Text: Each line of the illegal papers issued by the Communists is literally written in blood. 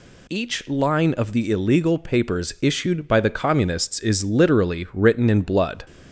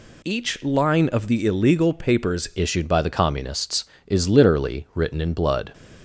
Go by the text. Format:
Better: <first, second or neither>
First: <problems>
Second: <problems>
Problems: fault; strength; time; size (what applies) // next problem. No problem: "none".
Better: first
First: none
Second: changes voice at "issued"; from 2.5 s on; 3.2 s long